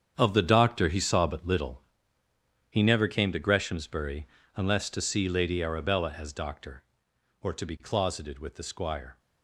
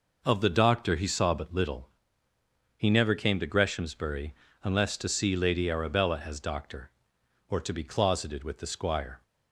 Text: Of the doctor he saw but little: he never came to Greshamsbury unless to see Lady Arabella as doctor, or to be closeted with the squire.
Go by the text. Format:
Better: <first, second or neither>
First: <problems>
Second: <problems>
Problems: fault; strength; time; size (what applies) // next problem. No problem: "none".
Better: second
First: gets quieter; strong; throughout; 11.5 dB // pauses between "Greshamsbury" and "unless"; slight; at 4.2 s; 0.28 s long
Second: pauses between "Greshamsbury" and "unless"; slight; at 4.3 s; 0.28 s long